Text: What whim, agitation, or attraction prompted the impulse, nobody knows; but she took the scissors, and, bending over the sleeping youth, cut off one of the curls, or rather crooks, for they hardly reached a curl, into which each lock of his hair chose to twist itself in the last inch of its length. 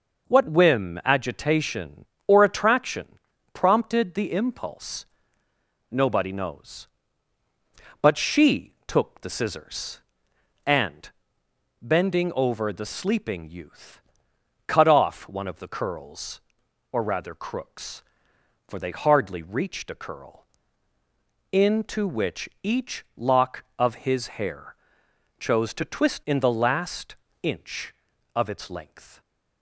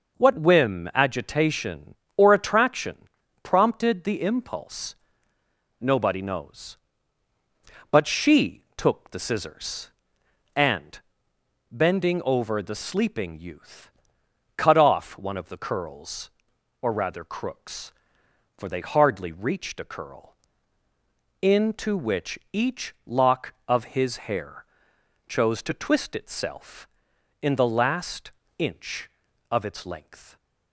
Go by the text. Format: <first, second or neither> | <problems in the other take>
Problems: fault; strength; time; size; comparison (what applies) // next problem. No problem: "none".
second | pauses between "attraction" and "prompted"; slight; at 3.1 s; 0.34 s long; slight in the second // pauses between "which" and "each"; slight; at 22.4 s; 0.16 s long; slight in the second // pauses between "hair" and "chose"; noticeable; at 24.7 s; 0.64 s long; noticeable in the second // skips "itself"; at 26.2 s // pauses between "last" and "inch"; slight; at 27.1 s; 0.28 s long; slight in the second